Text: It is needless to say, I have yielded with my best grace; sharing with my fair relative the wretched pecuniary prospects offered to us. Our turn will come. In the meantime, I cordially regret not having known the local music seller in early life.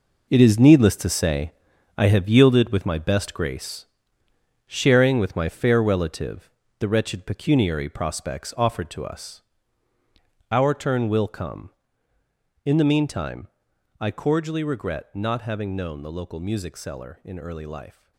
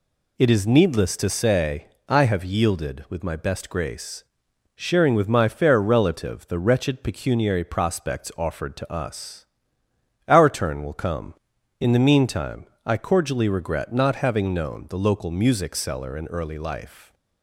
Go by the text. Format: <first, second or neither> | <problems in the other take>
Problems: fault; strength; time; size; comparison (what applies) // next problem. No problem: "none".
second | gets quieter; strong; throughout; 11.5 dB // pauses between "relative" and "the"; slight; at 6.4 s; 0.30 s long